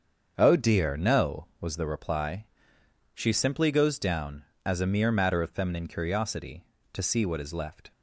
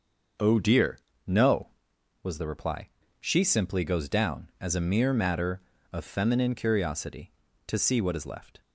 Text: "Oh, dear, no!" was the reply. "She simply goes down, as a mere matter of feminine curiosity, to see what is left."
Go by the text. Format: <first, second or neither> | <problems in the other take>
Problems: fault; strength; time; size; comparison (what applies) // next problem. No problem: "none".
neither | starts louder than the rest; the same in both